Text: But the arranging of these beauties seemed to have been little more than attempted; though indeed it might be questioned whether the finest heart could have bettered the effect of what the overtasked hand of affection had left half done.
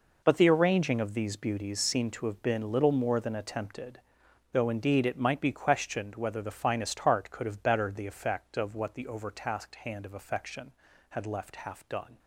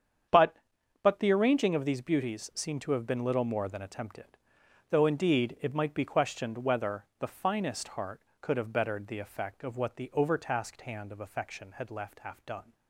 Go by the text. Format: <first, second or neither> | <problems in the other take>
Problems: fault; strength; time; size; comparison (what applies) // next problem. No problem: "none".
first | starts louder than the rest; strong; until 1.7 s; 8 dB // says "But" twice; at 1.0 s